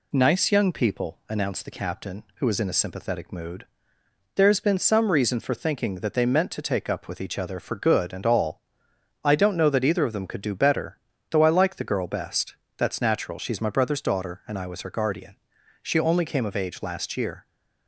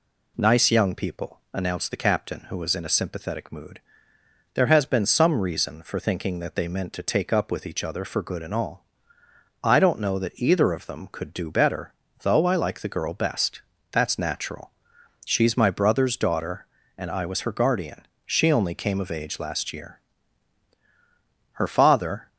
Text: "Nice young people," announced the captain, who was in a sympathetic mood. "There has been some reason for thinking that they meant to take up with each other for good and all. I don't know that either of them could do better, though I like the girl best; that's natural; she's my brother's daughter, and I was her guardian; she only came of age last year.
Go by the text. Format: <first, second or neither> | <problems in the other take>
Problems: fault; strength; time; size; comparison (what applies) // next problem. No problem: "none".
first | goes on to say "Her father"; noticeable; from 21.5 s on; 0.74 s long